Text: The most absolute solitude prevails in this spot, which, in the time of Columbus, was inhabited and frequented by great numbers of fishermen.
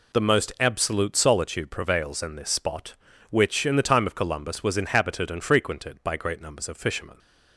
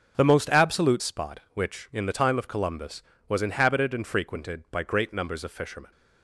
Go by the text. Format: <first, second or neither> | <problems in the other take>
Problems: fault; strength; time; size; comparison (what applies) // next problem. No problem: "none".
first | starts louder than the rest; until 1.1 s; 7 dB // skips "solitude prevails in this"; at 1.0 s